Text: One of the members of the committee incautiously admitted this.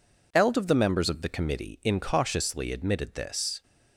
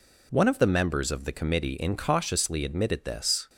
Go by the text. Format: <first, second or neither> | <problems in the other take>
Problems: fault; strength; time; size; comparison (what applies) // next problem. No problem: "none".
second | says "Eld" for "One"; at 0.3 s